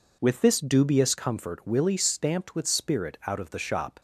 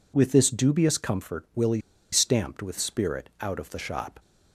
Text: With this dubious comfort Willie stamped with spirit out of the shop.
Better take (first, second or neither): first